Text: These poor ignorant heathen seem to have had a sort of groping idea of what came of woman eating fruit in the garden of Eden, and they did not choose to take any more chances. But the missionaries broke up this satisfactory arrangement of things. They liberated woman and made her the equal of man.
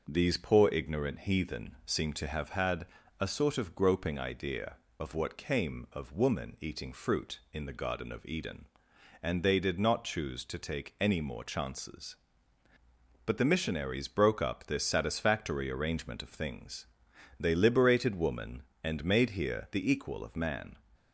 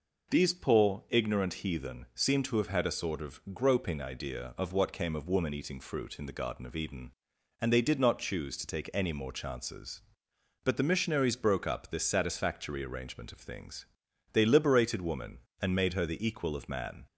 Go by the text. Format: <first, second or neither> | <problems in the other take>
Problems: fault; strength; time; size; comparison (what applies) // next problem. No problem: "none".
second | pauses between "had" and "a"; slight; at 2.8 s; 0.34 s long // says "here" for "her"; at 19.3 s